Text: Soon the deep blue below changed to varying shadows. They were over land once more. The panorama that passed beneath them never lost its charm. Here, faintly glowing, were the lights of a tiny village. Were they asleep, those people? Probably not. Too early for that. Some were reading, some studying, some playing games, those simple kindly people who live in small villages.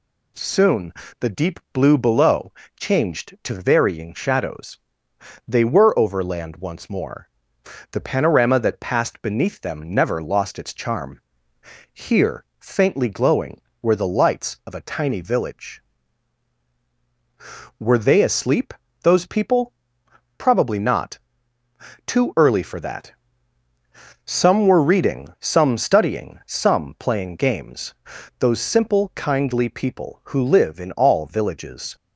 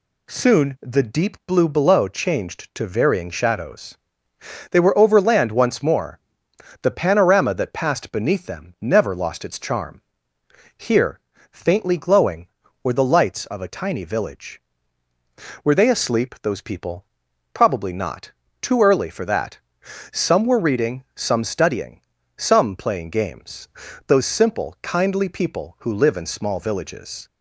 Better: second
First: pauses between "Soon" and "the"; slight; at 0.9 s; 0.26 s long // pauses between "below" and "changed"; slight; at 2.5 s; 0.26 s long // says "all" for "small"; at 30.9 s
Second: none

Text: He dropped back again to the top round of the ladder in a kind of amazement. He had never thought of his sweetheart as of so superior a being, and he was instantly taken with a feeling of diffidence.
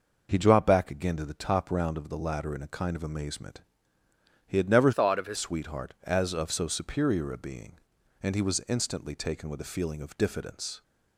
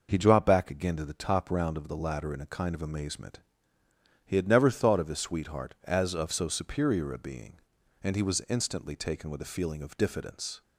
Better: second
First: changes voice from "thought" to "his"; from 4.9 to 5.3 s; 0.4 s long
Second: none

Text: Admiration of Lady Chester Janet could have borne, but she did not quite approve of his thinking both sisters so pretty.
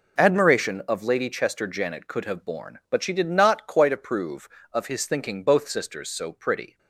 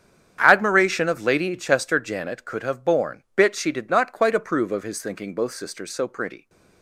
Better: first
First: none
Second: starts louder than the rest; strong; until 1.4 s; 8.5 dB // says "bit" for "but"; at 3.3 s

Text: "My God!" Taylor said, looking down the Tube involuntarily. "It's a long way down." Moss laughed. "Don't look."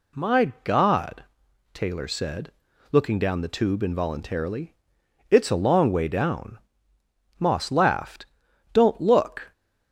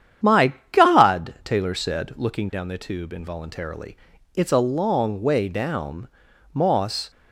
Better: first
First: none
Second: starts louder than the rest; strong; until 1.5 s; 9 dB // pauses between "My" and "God"; slight; at 0.5 s; 0.18 s long // stops before "laughed Don't look"; at 7.1 s

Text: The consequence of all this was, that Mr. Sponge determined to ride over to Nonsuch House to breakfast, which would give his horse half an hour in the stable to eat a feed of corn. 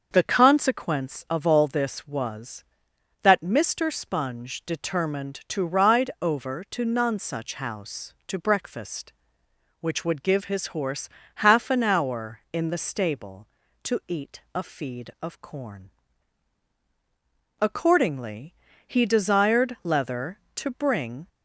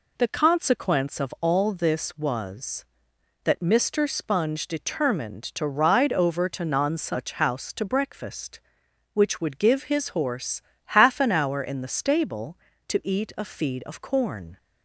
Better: second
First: starts louder than the rest; until 1.1 s; 6.5 dB // pauses between "horse" and "half"; slight; at 11.0 s; 0.28 s long // goes on to say "Accordingly he desired Leather to bring"; strong; from 17.5 s on; 3.6 s long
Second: pauses between "horse" and "half"; slight; at 10.6 s; 0.34 s long

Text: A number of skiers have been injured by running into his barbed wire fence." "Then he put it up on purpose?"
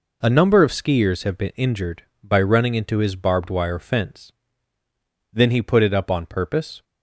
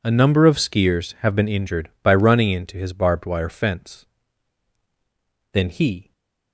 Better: first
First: none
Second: stays silent after the last word; slight; from 6.0 s on; 0.5 s long // stops before "put it up on purpose"; at 6.1 s

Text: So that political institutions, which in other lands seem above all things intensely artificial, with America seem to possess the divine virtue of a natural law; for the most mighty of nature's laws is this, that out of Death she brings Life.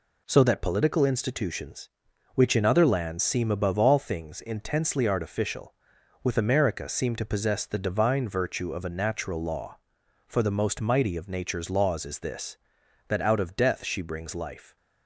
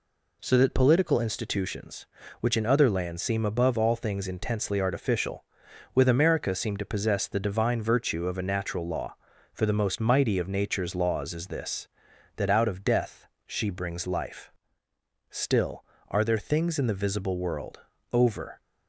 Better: first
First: none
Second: pauses between "Death" and "she"; slight; at 13.2 s; 0.20 s long // goes on to say "Still are there things in the visible world over"; strong; from 15.2 s on; 3.3 s long

